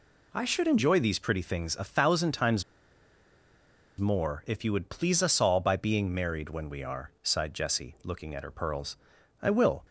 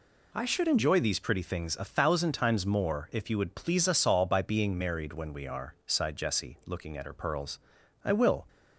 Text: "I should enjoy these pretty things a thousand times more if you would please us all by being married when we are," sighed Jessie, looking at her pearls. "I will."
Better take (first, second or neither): second